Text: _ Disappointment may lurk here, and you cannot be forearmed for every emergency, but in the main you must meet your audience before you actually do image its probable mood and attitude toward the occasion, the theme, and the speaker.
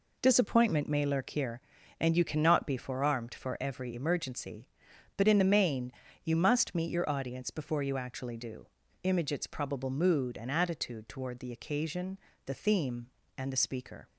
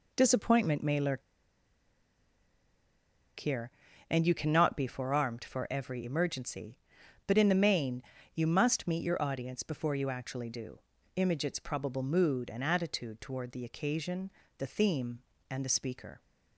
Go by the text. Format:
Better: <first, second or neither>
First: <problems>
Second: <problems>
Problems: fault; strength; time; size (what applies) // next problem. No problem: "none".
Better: first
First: pauses between "main" and "you"; slight; at 5.9 s; 0.30 s long // pauses between "do" and "image"; slight; at 8.6 s; 0.36 s long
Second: pauses between "lurk" and "here"; strong; at 1.2 s; 2.1 s long // pauses between "main" and "you"; slight; at 8.0 s; 0.30 s long // pauses between "do" and "image"; slight; at 10.7 s; 0.36 s long